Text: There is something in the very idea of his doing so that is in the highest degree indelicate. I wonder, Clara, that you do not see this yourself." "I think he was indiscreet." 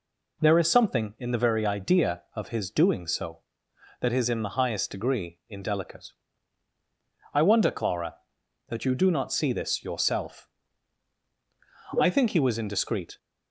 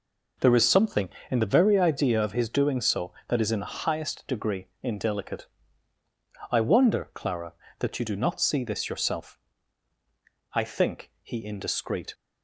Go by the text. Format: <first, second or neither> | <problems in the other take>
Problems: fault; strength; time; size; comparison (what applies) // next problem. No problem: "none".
first | pauses between "degree" and "indelicate"; slight; at 4.6 s; 0.16 s long // skips "was"; at 11.4 s